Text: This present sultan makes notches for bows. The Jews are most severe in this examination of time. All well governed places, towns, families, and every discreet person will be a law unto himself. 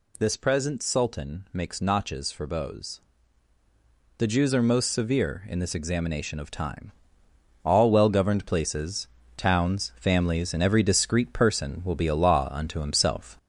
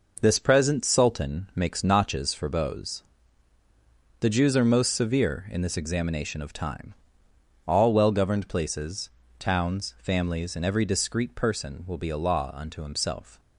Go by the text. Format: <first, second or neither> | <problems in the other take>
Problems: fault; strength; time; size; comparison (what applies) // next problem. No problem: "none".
second | gets louder; throughout; 3.5 dB